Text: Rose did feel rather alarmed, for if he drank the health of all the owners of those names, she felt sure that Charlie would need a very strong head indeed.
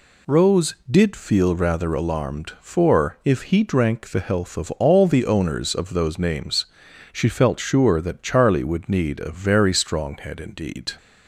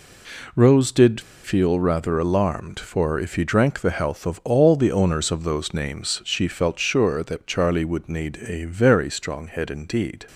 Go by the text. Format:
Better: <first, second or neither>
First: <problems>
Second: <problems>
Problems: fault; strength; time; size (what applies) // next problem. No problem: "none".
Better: first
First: none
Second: pauses between "did" and "feel"; slight; at 1.1 s; 0.23 s long